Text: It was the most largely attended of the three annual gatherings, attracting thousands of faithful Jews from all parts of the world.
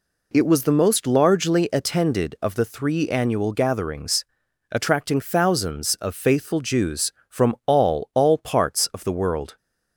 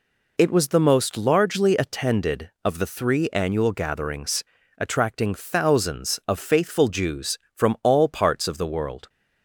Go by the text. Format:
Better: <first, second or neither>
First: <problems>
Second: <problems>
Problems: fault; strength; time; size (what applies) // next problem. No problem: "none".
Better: second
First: says "all" twice; at 8.1 s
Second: none